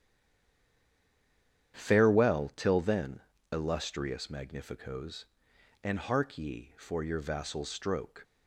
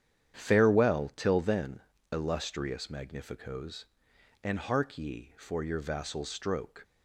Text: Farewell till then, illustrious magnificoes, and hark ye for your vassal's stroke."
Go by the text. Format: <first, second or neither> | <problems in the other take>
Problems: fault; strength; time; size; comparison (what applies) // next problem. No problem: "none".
second | stays silent before the first word; noticeable; until 1.7 s; 1.7 s long // starts louder than the rest; strong; until 2.7 s; 9 dB; strong in the second